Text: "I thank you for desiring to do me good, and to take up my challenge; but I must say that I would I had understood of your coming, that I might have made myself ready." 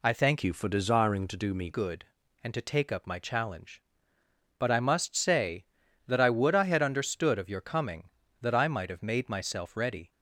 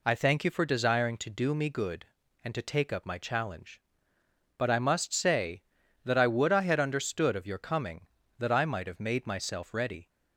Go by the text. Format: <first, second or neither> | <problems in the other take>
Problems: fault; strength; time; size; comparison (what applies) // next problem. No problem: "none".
second | changes voice from "you" to "me"; from 0.4 to 1.6 s; 1.2 s long